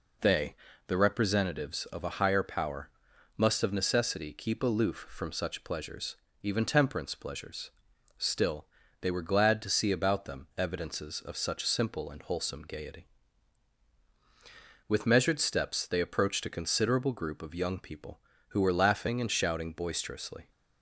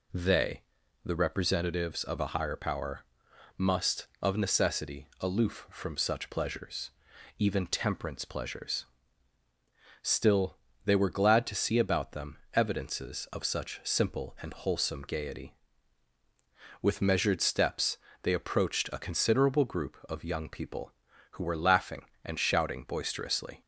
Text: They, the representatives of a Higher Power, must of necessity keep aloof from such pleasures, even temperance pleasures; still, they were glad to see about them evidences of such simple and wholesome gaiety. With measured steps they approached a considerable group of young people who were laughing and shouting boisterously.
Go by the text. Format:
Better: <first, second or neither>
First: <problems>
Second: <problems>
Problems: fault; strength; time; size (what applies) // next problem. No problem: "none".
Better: first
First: none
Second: skips "keep"; at 5.1 s // pauses between "steps" and "they"; slight; at 17.9 s; 0.26 s long